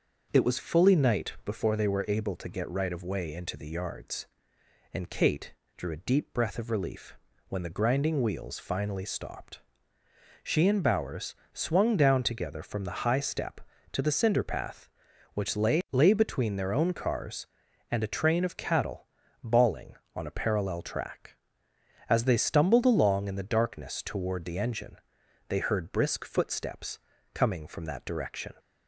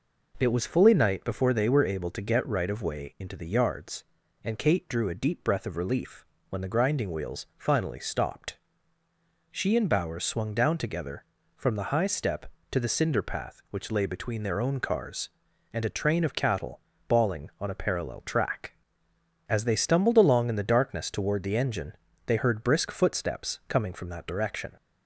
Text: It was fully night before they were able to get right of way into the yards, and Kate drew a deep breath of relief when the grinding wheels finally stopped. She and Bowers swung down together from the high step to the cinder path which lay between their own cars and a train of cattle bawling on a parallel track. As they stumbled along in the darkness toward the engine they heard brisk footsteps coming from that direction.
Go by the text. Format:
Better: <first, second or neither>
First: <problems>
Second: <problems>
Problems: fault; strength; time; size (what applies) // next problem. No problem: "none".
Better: second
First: starts louder than the rest; until 1.3 s; 6.5 dB // pauses between "Kate" and "drew"; slight; at 5.5 s; 0.22 s long // pauses between "relief" and "when"; slight; at 7.1 s; 0.32 s long // pauses between "Bowers" and "swung"; slight; at 11.3 s; 0.18 s long // says "lay" twice; at 15.9 s // pauses between "cattle" and "bawling"; slight; at 19.0 s; 0.34 s long // pauses between "engine" and "they"; noticeable; at 24.9 s; 0.50 s long // pauses between "footsteps" and "coming"; slight; at 26.9 s; 0.34 s long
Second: pauses between "relief" and "when"; slight; at 6.2 s; 0.24 s long // pauses between "cattle" and "bawling"; slight; at 16.7 s; 0.28 s long // pauses between "engine" and "they"; slight; at 21.9 s; 0.32 s long